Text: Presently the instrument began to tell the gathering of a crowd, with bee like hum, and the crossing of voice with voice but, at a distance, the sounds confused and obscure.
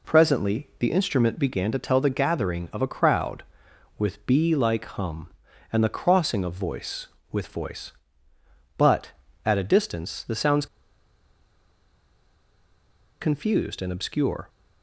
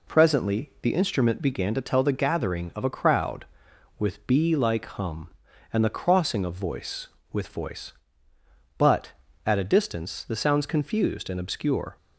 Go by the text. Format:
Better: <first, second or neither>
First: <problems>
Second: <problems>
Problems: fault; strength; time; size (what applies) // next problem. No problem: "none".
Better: second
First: pauses between "sounds" and "confused"; strong; at 10.6 s; 2.5 s long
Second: none